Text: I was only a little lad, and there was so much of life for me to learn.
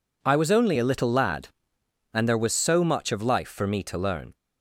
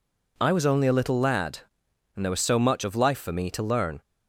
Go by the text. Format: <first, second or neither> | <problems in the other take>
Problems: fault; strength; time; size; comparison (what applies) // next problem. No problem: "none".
neither | none